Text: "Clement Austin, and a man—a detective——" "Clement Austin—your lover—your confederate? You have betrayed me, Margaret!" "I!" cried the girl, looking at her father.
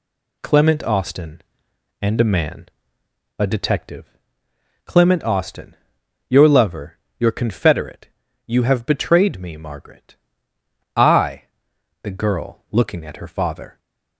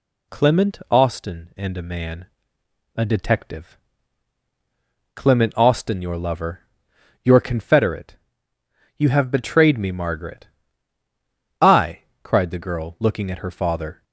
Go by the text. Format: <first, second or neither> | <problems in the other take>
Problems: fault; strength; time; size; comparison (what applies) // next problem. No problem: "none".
second | skips "cried"; at 11.7 s